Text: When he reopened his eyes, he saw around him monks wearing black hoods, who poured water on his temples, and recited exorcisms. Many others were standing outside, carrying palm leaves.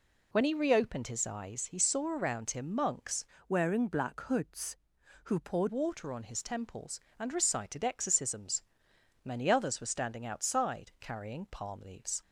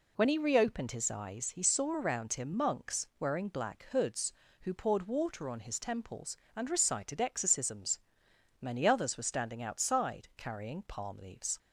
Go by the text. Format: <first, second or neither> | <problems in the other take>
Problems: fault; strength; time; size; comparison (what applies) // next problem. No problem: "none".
second | changes voice from "wearing" to "poured"; from 3.4 to 5.6 s; 2.2 s long